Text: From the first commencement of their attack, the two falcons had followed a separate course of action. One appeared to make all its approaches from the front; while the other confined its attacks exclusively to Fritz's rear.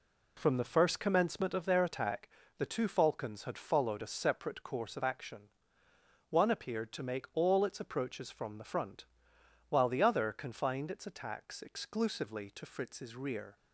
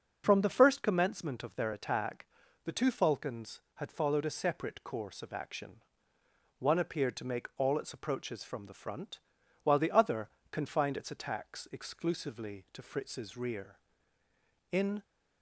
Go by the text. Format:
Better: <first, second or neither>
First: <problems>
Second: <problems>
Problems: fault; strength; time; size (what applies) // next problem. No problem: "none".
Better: first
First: none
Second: starts louder than the rest; noticeable; until 1.2 s; 6 dB // pauses between "other" and "confined"; slight; at 10.3 s; 0.20 s long // goes on to say "In"; slight; from 14.7 s on; 0.30 s long